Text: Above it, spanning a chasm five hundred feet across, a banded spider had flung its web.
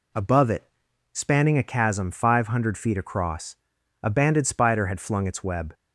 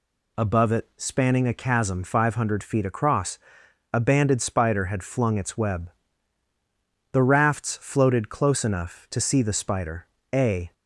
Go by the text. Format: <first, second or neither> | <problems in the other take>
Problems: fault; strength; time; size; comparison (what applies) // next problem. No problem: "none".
first | goes on to say "The rafts floated close enough to see the spider a"; strong; from 7.1 s on; 3.6 s long